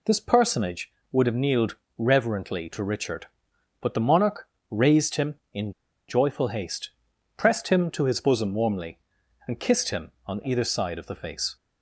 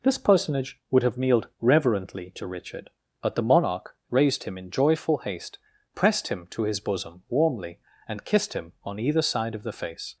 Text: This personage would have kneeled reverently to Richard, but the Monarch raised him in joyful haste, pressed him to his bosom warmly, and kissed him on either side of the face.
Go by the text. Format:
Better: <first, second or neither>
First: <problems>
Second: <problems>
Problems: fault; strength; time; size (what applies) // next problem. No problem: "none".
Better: second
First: pauses between "kneeled" and "reverently"; slight; at 1.7 s; 0.20 s long // pauses between "Monarch" and "raised"; slight; at 4.4 s; 0.20 s long // pauses between "in" and "joyful"; at 5.7 s; 0.37 s long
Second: pauses between "Monarch" and "raised"; slight; at 3.9 s; 0.15 s long